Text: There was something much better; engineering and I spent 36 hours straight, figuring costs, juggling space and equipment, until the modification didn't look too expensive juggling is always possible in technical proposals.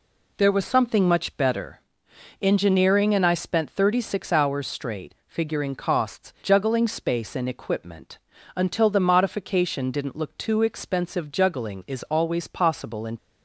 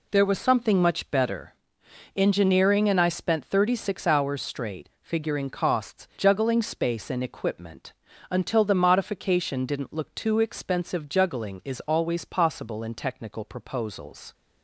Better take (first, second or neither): second